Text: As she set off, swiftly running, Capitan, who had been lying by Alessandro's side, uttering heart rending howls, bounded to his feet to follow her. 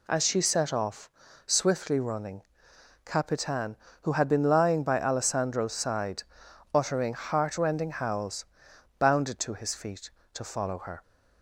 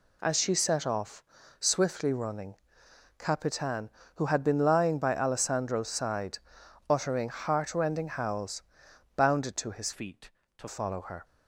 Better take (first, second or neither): first